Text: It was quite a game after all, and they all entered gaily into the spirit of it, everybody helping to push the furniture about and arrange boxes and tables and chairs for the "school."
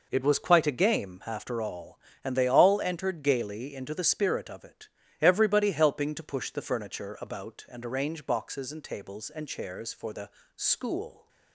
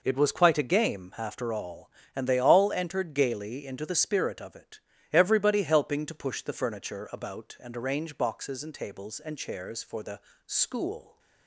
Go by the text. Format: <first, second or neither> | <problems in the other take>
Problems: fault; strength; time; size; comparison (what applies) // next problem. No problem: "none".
neither | pauses between "the" and "school"; slight; the same in both